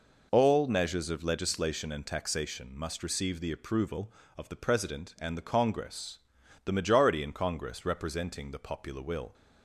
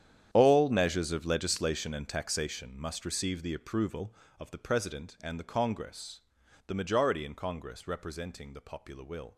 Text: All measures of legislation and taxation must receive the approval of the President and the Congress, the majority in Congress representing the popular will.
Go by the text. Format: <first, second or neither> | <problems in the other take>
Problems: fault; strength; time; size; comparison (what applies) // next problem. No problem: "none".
first | gets quieter; strong; throughout; 15.5 dB